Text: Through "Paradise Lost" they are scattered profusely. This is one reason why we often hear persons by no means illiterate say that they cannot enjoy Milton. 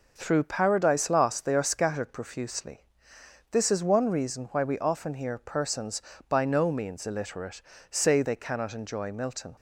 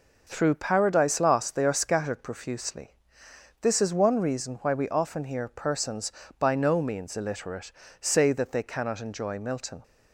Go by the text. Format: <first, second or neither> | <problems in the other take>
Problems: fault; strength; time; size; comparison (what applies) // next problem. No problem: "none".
second | pauses between "illiterate" and "say"; slight; at 7.6 s; 0.30 s long; slight in the second // skips "that"; at 8.2 s